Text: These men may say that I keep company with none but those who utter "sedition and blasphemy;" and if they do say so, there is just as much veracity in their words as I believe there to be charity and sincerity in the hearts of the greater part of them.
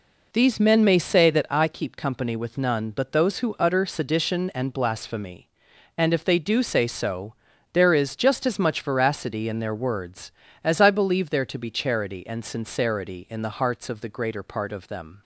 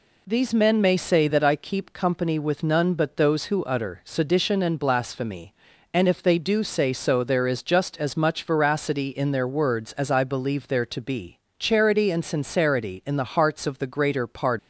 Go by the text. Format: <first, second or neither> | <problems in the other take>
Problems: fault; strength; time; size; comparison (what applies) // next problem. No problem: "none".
first | pauses between "be" and "charity"; slight; at 11.3 s; 0.20 s long // stops before "of them"; at 14.5 s